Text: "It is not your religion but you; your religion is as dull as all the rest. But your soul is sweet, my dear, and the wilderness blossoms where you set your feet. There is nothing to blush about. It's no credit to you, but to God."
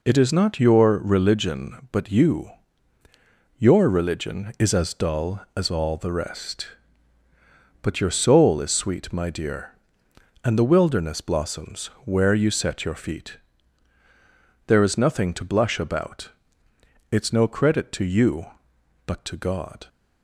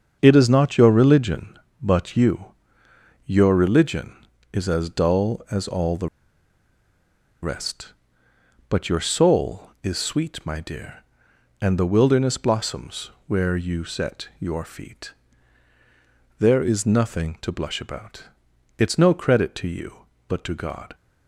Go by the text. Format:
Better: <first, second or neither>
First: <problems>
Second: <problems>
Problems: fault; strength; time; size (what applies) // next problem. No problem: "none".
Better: first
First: pauses between "blossoms" and "where"; slight; at 11.8 s; 0.18 s long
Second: starts louder than the rest; until 1.2 s; 7 dB // pauses between "the" and "rest"; strong; at 6.0 s; 1.3 s long // pauses between "blossoms" and "where"; slight; at 13.1 s; 0.16 s long